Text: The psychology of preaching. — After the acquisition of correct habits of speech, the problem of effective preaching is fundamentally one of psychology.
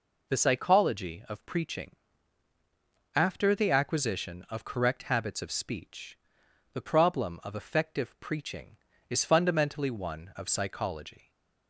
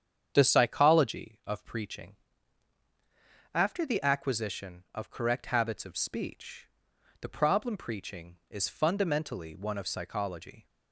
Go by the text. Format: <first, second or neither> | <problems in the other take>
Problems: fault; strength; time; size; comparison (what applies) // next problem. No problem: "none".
first | starts louder than the rest; strong; until 1.3 s; 8 dB // skips "of effective"; at 7.7 s